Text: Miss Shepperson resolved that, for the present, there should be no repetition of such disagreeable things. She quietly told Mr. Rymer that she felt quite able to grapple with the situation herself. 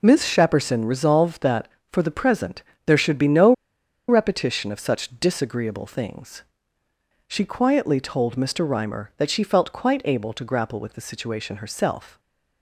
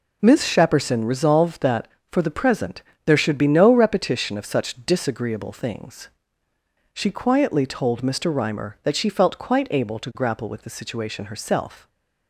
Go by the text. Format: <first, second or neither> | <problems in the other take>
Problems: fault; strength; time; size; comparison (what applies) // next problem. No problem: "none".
second | pauses between "no" and "repetition"; noticeable; at 3.5 s; 0.56 s long